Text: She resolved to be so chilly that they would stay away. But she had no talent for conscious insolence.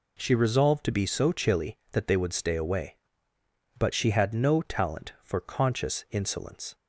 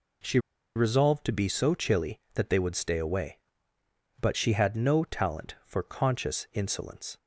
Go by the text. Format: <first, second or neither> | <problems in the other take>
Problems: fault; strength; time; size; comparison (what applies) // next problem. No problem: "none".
first | pauses between "She" and "resolved"; at 0.3 s; 0.37 s long